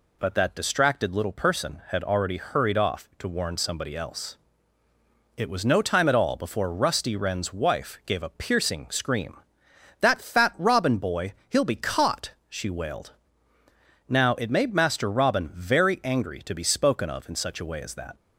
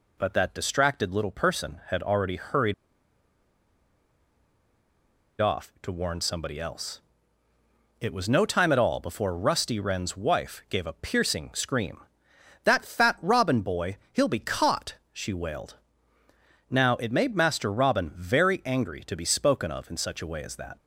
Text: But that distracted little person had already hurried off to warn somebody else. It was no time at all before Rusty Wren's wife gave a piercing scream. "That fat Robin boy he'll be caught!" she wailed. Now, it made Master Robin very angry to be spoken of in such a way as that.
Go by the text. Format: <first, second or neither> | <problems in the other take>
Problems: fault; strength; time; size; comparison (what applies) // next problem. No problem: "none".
first | pauses between "hurried" and "off"; strong; at 2.7 s; 2.6 s long // pauses between "boy" and "he'll"; slight; at 13.9 s; 0.16 s long; slight in the first